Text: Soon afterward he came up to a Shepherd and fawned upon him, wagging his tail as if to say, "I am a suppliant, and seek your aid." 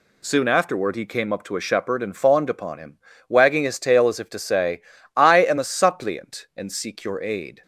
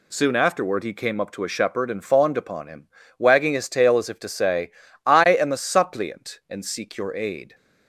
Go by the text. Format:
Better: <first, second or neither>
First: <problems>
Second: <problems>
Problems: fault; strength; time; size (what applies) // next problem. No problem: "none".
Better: neither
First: none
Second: none